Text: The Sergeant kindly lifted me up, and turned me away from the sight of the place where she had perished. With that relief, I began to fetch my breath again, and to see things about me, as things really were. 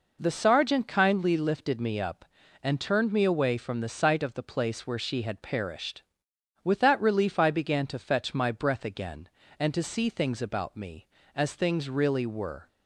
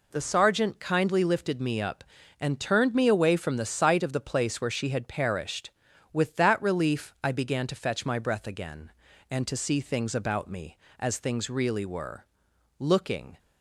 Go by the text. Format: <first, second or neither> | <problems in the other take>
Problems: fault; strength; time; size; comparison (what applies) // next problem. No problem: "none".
first | goes on to say "Looking"; from 12.7 s on; 0.60 s long